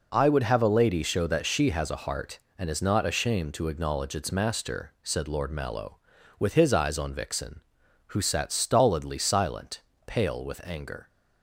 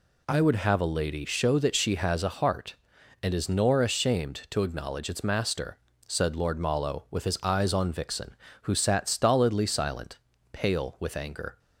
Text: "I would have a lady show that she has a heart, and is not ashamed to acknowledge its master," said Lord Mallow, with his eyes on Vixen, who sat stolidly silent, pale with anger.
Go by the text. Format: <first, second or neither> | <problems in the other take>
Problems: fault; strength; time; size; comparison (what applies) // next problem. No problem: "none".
first | says "nor" for "not"; at 3.4 s